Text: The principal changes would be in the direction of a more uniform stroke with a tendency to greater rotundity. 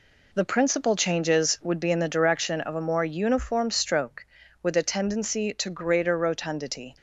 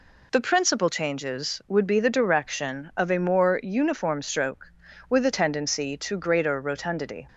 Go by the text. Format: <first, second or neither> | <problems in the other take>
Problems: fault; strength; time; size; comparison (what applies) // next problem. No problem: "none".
first | skips "in"; at 2.0 s